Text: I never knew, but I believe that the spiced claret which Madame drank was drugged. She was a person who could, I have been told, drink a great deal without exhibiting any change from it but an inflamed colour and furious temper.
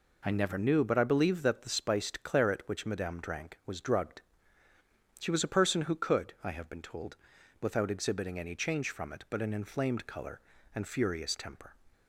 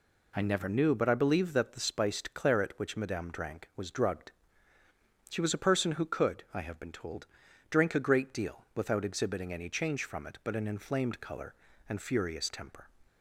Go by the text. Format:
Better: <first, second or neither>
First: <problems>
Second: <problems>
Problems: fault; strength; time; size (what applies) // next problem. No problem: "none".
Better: second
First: skips "drink a great deal"; at 7.3 s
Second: none